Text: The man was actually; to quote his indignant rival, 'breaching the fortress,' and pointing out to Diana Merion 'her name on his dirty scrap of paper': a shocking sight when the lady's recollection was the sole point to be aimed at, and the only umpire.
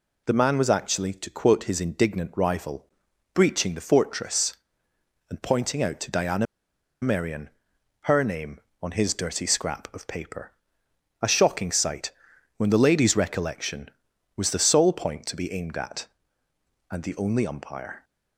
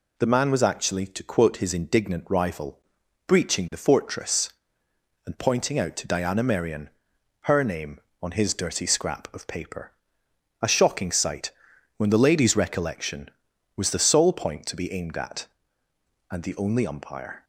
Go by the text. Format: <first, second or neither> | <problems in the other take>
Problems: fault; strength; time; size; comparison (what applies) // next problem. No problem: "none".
second | pauses between "Diana" and "Merion"; noticeable; at 6.4 s; 0.56 s long // pauses between "Merion" and "her"; noticeable; at 7.4 s; 0.54 s long; noticeable in the second // pauses between "sight" and "when"; noticeable; at 12.0 s; 0.48 s long; noticeable in the second